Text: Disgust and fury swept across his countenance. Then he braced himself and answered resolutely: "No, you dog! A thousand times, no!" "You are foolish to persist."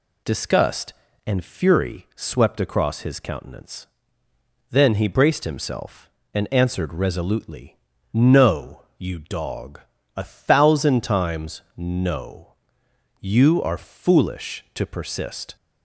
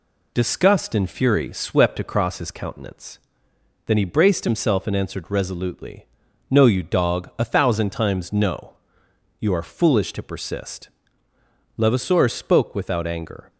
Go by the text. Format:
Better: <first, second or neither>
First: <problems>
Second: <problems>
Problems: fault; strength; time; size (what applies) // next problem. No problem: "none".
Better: first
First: none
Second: goes on to say "Levasseur spoke without anger"; strong; from 11.7 s on; 1.7 s long